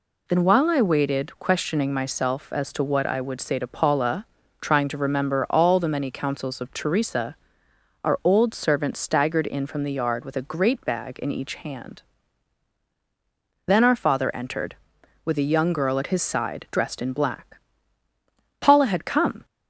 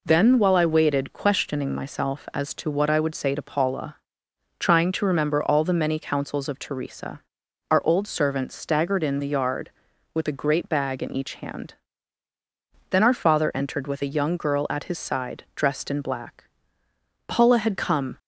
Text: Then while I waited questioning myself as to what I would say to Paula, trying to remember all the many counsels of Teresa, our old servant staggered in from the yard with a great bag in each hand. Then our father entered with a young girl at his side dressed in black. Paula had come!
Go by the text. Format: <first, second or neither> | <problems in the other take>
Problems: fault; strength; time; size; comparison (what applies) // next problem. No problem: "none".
first | skips "from"; at 9.2 s